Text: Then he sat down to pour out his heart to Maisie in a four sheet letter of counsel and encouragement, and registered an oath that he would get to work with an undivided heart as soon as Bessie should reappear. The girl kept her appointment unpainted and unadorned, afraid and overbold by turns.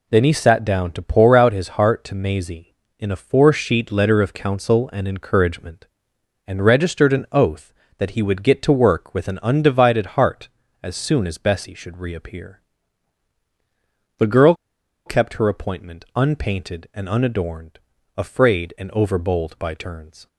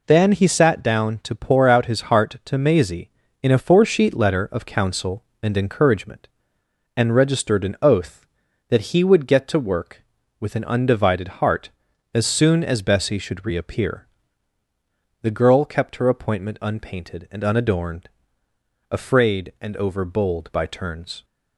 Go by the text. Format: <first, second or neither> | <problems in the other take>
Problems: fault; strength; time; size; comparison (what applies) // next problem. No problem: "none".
second | pauses between "girl" and "kept"; noticeable; at 14.5 s; 0.52 s long